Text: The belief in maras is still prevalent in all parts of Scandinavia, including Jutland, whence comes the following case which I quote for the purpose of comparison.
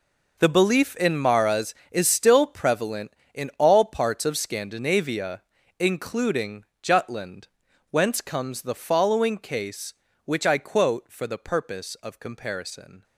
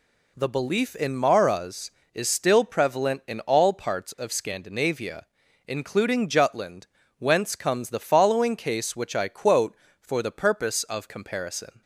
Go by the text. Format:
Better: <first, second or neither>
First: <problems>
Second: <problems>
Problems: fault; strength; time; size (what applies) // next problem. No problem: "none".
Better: second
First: gets quieter; strong; throughout; 13 dB // pauses between "including" and "Jutland"; slight; at 6.6 s; 0.18 s long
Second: none